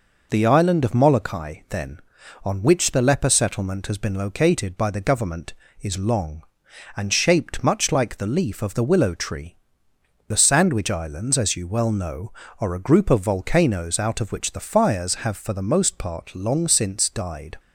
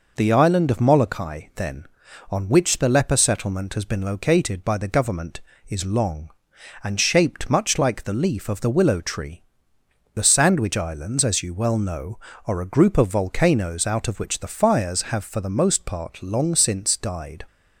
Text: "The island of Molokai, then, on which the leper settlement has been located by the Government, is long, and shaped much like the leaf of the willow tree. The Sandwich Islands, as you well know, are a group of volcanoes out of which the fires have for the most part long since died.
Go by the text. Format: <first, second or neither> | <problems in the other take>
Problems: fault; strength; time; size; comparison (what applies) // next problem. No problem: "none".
neither | none